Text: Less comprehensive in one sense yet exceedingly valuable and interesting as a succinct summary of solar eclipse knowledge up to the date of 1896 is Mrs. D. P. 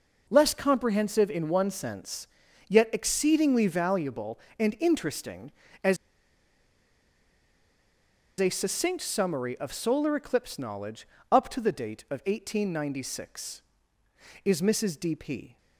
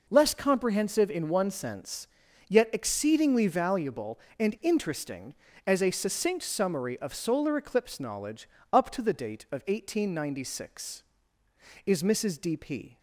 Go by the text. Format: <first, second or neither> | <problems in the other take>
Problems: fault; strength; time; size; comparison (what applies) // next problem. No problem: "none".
second | pauses between "sense" and "yet"; at 2.2 s; 0.40 s long; also in the second // pauses between "as" and "a"; strong; at 5.9 s; 2.4 s long // pauses between "knowledge" and "up"; slight; at 11.0 s; 0.24 s long; slight in the second